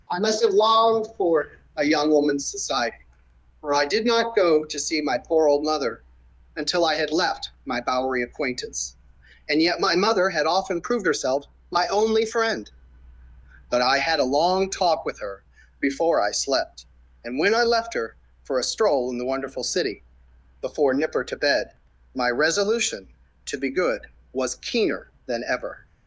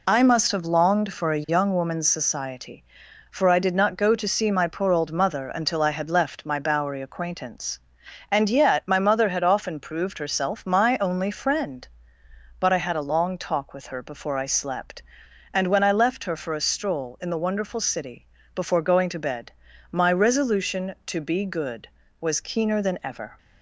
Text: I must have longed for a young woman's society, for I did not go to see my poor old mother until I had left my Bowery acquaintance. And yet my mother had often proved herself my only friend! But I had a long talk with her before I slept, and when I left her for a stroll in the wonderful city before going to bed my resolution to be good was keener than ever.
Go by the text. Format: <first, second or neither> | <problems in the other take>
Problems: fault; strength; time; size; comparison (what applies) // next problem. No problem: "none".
second | pauses between "for" and "a"; slight; at 1.5 s; 0.26 s long // pauses between "mother" and "until"; noticeable; at 6.0 s; 0.54 s long // pauses between "left" and "my"; slight; at 7.5 s; 0.16 s long // pauses between "herself" and "my"; slight; at 11.4 s; 0.28 s long // pauses between "her" and "before"; at 15.4 s; 0.38 s long // pauses between "city" and "before"; noticeable; at 20.0 s; 0.58 s long; slight in the second // says "nipper" for "going"; at 20.9 s // pauses between "bed" and "my"; at 21.7 s; 0.42 s long; also in the second